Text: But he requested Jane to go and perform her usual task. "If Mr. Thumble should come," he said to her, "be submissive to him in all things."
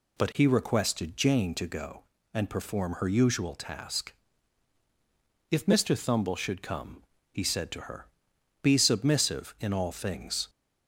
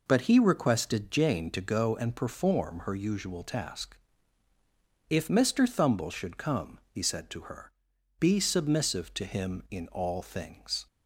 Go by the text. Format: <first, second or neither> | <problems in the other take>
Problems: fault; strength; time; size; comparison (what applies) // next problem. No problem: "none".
second | skips "to him"; at 9.5 s